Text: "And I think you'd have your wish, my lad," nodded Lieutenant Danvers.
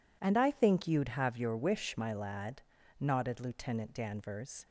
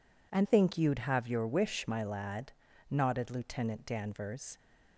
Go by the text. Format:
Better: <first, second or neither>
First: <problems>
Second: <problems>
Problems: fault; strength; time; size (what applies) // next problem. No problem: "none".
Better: first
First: none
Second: skips "I"; at 0.4 s